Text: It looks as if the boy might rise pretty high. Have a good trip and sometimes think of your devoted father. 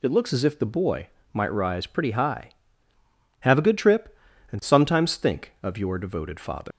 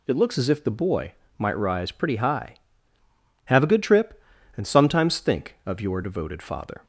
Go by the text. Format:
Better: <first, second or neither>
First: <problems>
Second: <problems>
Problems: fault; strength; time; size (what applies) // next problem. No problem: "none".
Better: second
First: pauses between "boy" and "might"; slight; at 1.0 s; 0.24 s long // leaves "father" unfinished; at 6.7 s; 115 ms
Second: pauses between "boy" and "might"; slight; at 1.1 s; 0.24 s long